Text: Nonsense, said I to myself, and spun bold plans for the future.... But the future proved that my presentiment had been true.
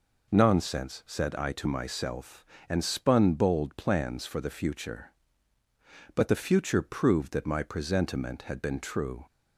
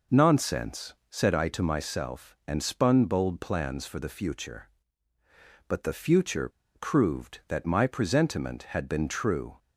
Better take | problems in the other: first | pauses between "future" and "proved"; slight; at 6.4 s; 0.26 s long

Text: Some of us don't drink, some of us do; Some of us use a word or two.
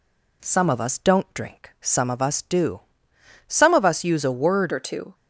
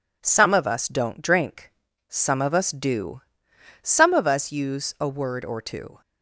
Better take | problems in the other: second | changes voice at "or"; from 4.7 s on; 0.4 s long

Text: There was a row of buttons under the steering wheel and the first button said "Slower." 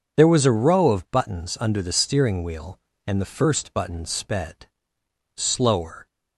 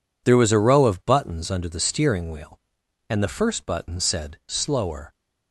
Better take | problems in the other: second | says "sped" for "said"; at 4.0 s

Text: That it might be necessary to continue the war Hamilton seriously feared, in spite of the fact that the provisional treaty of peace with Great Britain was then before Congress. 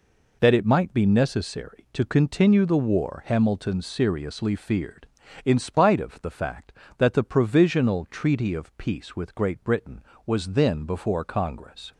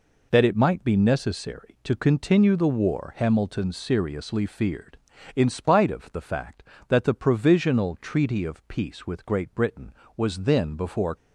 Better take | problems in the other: first | stops before "Congress"; at 11.1 s

